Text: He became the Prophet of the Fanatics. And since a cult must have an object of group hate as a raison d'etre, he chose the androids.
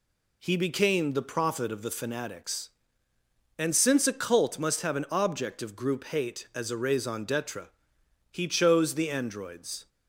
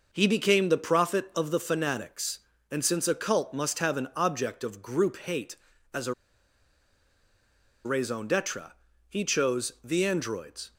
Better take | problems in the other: first | pauses between "a" and "raison"; strong; at 6.1 s; 1.7 s long

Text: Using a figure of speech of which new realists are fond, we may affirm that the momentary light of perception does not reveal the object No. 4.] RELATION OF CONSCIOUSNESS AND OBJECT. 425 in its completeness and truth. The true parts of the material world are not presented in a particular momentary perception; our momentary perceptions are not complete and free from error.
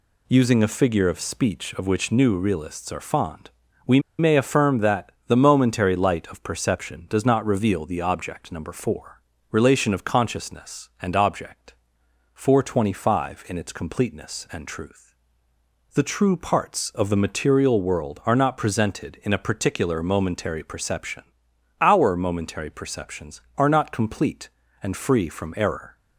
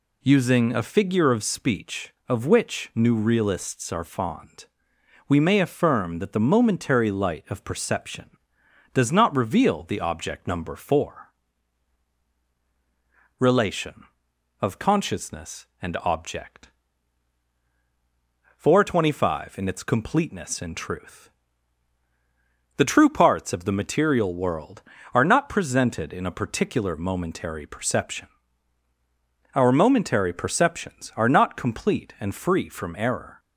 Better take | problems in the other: second | pauses between "we" and "may"; slight; at 3.9 s; 0.19 s long // pauses between "that" and "the"; slight; at 5.1 s; 0.18 s long

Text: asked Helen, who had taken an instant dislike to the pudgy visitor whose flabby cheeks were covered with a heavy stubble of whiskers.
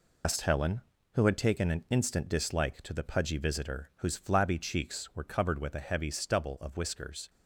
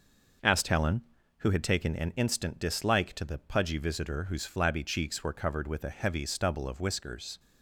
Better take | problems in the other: second | loses the start of "asked"; at 0.2 s; 100 ms

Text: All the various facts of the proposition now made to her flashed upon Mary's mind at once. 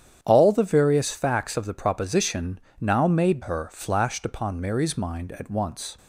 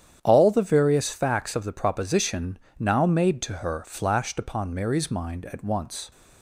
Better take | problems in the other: second | starts louder than the rest; strong; until 1.2 s; 9 dB; strong in the second // pauses between "proposition" and "now"; slight; at 2.5 s; 0.20 s long; slight in the second // skips "to"; at 3.4 s

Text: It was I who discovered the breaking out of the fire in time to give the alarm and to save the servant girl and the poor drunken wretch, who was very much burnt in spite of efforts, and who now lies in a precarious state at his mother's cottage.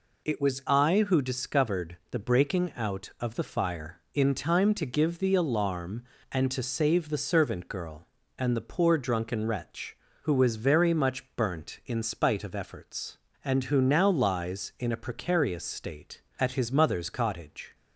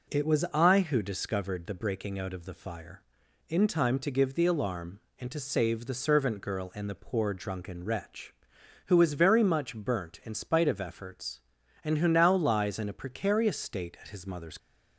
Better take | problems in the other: first | stops before "cottage"; at 14.5 s

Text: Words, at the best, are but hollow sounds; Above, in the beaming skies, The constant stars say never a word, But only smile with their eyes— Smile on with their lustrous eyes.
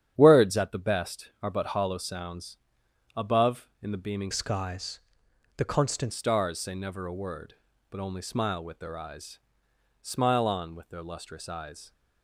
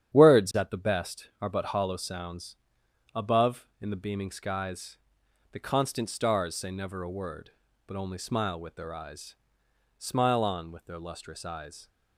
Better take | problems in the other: second | starts louder than the rest; strong; until 1.1 s; 9.5 dB; strong in the second // changes voice from "skies" to "constant"; from 4.3 to 6.1 s; 1.8 s long

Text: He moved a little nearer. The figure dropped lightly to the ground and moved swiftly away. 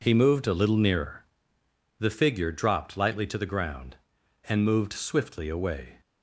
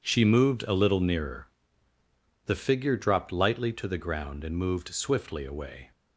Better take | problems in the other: first | says "She" for "He"; at 0.0 s

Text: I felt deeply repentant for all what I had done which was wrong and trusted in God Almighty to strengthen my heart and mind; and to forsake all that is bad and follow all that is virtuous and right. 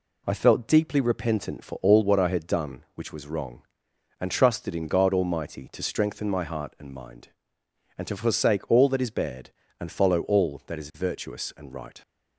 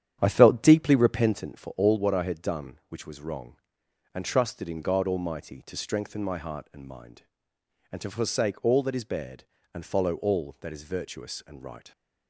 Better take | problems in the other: first | starts louder than the rest; strong; until 1.4 s; 9.5 dB

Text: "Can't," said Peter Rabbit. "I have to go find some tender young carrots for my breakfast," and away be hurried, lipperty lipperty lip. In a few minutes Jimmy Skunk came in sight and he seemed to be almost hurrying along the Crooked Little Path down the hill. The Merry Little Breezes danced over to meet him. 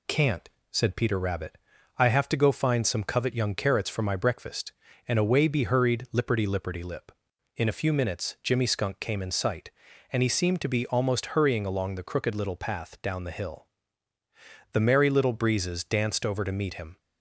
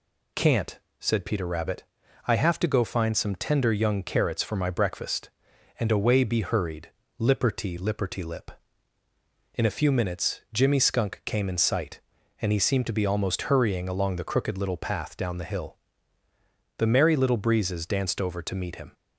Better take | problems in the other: second | says "covet" for "tender"; at 3.0 s

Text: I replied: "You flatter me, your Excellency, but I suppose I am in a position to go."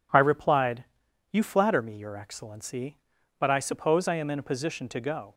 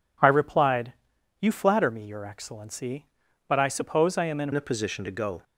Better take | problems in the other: first | changes voice at "a"; from 4.5 s on; 0.9 s long

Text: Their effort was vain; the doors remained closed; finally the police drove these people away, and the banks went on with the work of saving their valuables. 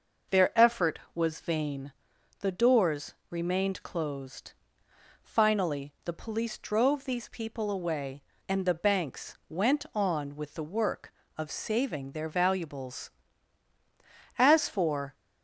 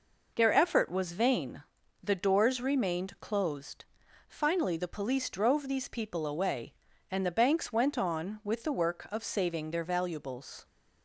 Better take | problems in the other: second | pauses between "doors" and "remained"; slight; at 3.1 s; 0.16 s long // goes on to say "As for"; noticeable; from 14.3 s on; 0.78 s long

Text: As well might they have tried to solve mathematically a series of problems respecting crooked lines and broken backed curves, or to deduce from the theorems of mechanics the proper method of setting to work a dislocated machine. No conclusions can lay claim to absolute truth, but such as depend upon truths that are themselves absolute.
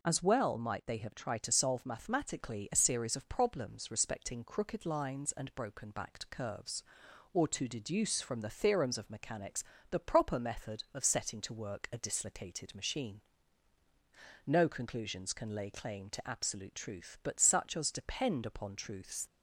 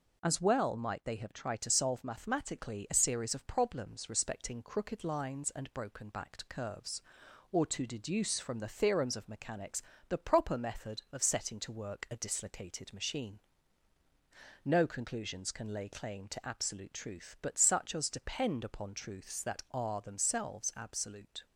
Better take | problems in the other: second | pauses between "mechanics" and "the"; slight; at 9.6 s; 0.28 s long; slight in the second // stops before "that are themselves absolute"; at 19.2 s

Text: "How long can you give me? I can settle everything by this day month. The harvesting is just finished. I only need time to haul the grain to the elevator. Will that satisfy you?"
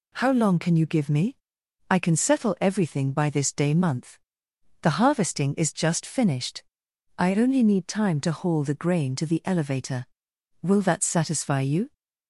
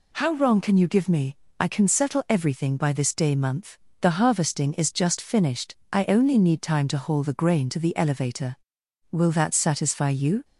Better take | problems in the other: first | says "wrong" for "long"; at 0.3 s

